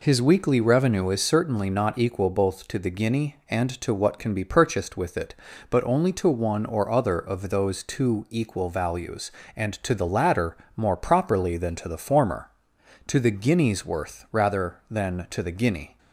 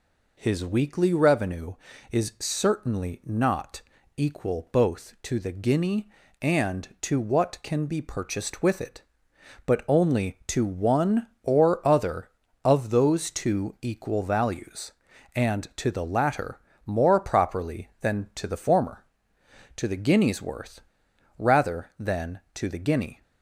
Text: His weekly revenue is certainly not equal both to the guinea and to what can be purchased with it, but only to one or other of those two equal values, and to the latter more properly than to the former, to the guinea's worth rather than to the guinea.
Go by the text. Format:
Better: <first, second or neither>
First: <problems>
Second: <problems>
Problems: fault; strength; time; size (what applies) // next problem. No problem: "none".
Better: first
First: pauses between "latter" and "more"; slight; at 10.5 s; 0.18 s long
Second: pauses between "not" and "equal"; slight; at 3.8 s; 0.36 s long // pauses between "latter" and "more"; slight; at 16.6 s; 0.26 s long // pauses between "worth" and "rather"; noticeable; at 20.8 s; 0.55 s long